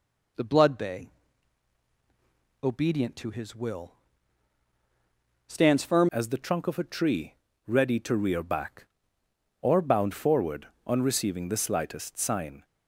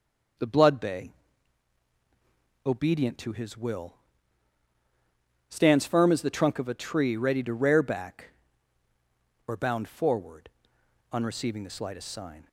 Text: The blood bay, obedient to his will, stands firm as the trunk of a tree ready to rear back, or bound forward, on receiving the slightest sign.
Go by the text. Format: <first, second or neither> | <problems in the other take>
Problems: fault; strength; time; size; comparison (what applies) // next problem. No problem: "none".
second | changes voice at "as"; from 6.1 s on; 6.5 s long // pauses between "tree" and "ready"; slight; at 7.3 s; 0.32 s long